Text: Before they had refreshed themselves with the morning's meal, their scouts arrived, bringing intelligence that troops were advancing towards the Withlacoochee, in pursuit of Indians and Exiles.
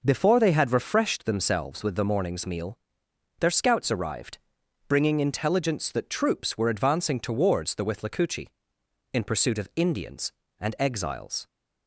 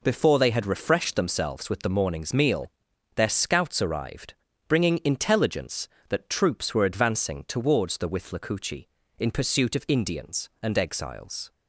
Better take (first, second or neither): neither